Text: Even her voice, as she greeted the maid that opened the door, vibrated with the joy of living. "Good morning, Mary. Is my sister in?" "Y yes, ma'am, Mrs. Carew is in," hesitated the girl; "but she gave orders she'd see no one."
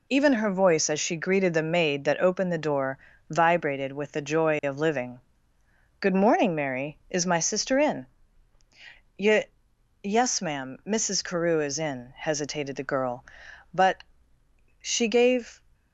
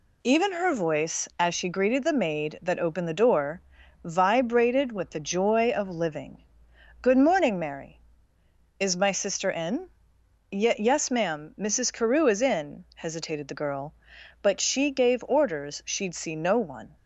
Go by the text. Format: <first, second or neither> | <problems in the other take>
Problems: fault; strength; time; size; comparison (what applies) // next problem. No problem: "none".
second | pauses between "Y" and "yes"; noticeable; at 9.4 s; 0.58 s long // pauses between "but" and "she"; noticeable; at 14.0 s; 0.78 s long // stops before "orders she'd see no one"; at 15.7 s